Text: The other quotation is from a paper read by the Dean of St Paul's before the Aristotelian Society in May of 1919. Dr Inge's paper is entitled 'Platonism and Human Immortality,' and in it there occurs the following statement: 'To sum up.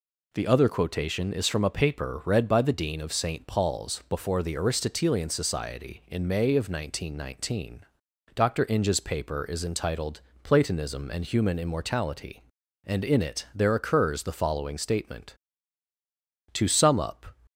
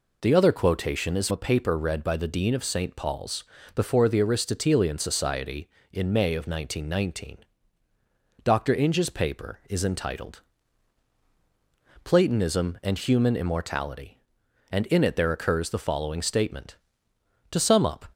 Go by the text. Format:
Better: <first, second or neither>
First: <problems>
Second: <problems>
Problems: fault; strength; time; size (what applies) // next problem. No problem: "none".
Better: first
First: pauses between "entitled" and "Platonism"; slight; at 10.2 s; 0.22 s long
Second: skips "from"; at 1.2 s // pauses between "Paul's" and "before"; slight; at 3.4 s; 0.32 s long // pauses between "entitled" and "Platonism"; strong; at 10.4 s; 1.6 s long